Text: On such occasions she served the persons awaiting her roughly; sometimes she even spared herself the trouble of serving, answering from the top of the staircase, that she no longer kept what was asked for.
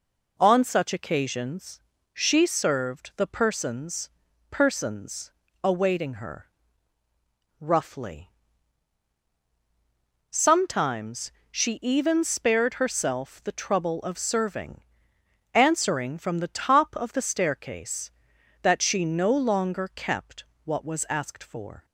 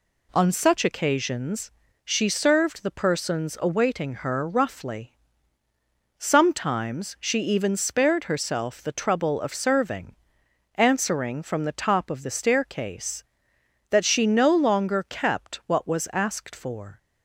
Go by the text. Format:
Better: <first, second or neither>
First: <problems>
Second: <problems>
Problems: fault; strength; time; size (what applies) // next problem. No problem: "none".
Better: second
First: pauses between "occasions" and "she"; slight; at 1.8 s; 0.32 s long // says "persons" twice; at 4.5 s // pauses between "her" and "roughly"; at 6.5 s; 1.0 s long // pauses between "sometimes" and "she"; slight; at 11.3 s; 0.18 s long // pauses between "kept" and "what"; slight; at 20.4 s; 0.22 s long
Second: pauses between "occasions" and "she"; slight; at 1.7 s; 0.32 s long